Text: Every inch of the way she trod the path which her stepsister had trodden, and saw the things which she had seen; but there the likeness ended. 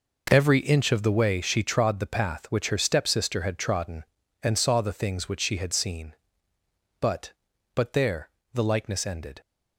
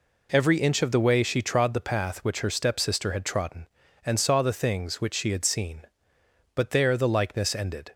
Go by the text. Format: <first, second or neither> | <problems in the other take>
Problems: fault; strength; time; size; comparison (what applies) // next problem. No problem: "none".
second | says "but" twice; at 7.7 s // pauses between "there" and "the"; slight; at 8.2 s; 0.24 s long